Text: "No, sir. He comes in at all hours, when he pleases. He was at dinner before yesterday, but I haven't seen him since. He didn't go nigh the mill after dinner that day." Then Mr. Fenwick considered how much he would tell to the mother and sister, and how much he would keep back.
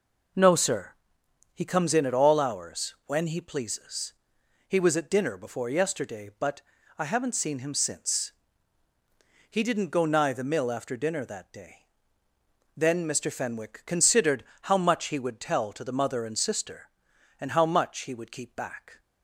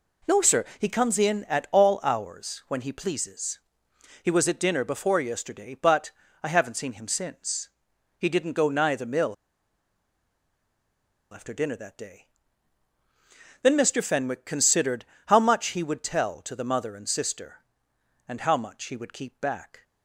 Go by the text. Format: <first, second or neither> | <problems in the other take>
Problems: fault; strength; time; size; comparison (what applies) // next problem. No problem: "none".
first | pauses between "but" and "I"; slight; at 6.1 s; 0.32 s long; slight in the first // pauses between "mill" and "after"; strong; at 9.3 s; 1.9 s long // pauses between "considered" and "how"; slight; at 15.0 s; 0.22 s long; slight in the first